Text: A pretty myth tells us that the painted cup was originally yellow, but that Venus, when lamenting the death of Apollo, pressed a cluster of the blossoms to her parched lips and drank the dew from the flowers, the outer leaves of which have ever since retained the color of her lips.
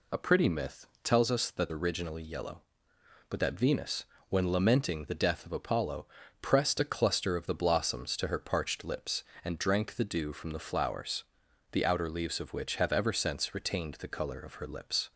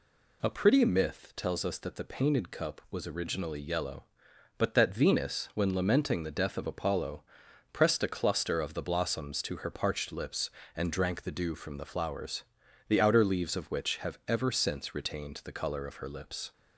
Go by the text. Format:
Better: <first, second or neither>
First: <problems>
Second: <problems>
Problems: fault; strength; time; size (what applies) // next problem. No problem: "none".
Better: second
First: pauses between "myth" and "tells"; slight; at 0.8 s; 0.16 s long // skips "the painted cup was"; at 1.6 s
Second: none